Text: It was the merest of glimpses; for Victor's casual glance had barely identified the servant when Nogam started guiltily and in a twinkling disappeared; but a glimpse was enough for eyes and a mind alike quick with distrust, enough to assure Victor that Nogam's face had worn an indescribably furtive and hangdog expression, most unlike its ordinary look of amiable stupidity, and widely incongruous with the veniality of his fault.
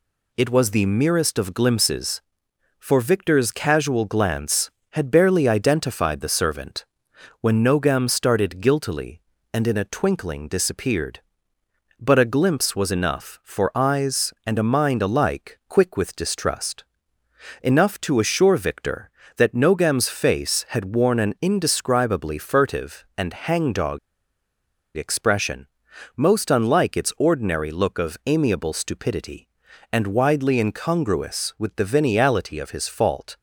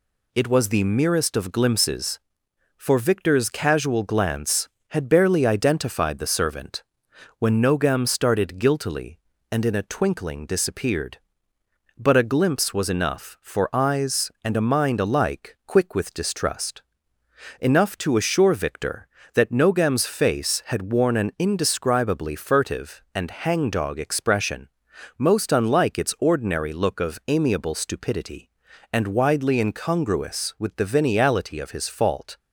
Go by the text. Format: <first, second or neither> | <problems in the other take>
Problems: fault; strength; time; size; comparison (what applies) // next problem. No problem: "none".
second | pauses between "servant" and "when"; noticeable; at 6.8 s; 0.56 s long; noticeable in the second // pauses between "hangdog" and "expression"; noticeable; at 23.9 s; 0.97 s long